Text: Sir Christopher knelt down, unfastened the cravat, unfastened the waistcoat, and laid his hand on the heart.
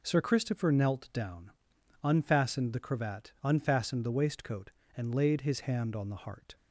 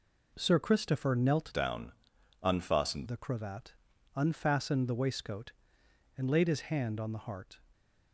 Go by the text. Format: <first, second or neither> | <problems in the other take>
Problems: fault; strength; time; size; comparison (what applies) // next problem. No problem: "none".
first | changes voice from "down" to "unfastened"; from 1.5 to 3.0 s; 1.5 s long